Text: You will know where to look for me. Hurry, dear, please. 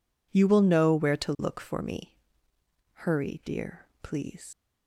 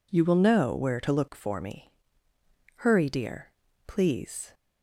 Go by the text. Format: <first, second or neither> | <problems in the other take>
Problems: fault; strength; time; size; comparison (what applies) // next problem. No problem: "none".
second | leaves "please" unfinished; at 4.5 s; 95 ms